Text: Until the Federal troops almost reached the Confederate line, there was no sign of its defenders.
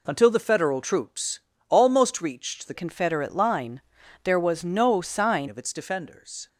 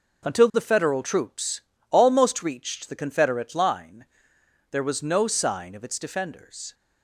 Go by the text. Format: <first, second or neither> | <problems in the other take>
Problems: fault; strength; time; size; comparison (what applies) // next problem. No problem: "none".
second | pauses between "troops" and "almost"; slight; at 1.4 s; 0.28 s long; slight in the second // changes voice from "Confederate" to "sign"; from 2.7 to 5.4 s; 2.7 s long